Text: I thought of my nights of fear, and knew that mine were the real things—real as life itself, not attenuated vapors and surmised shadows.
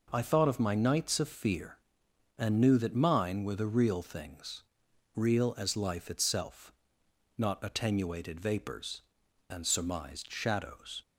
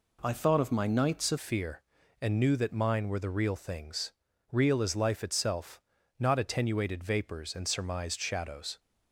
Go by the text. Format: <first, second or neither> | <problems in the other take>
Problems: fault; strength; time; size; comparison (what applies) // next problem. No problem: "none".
first | changes voice at "fear"; from 1.3 s on; 7.4 s long